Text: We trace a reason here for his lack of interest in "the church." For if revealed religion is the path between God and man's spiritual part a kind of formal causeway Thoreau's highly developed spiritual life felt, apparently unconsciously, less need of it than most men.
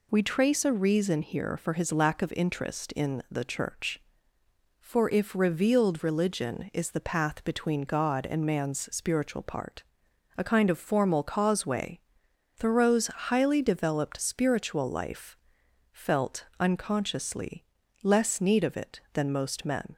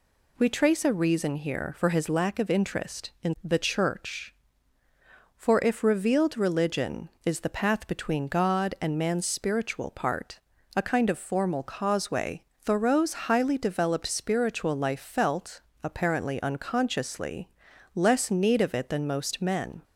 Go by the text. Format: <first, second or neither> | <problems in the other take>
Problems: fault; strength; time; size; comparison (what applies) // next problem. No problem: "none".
second | pauses between "part" and "a"; noticeable; at 9.8 s; 0.52 s long; slight in the second // pauses between "causeway" and "Thoreau's"; noticeable; at 11.9 s; 0.56 s long; slight in the second // pauses between "life" and "felt"; noticeable; at 15.3 s; 0.56 s long // skips "apparently"; at 16.5 s